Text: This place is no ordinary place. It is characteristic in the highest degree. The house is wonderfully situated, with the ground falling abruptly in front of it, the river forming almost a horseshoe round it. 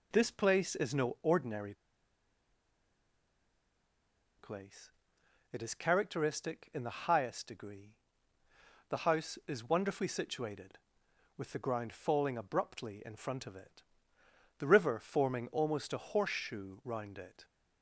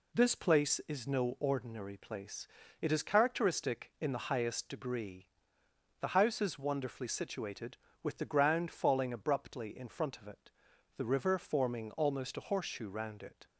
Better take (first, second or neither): second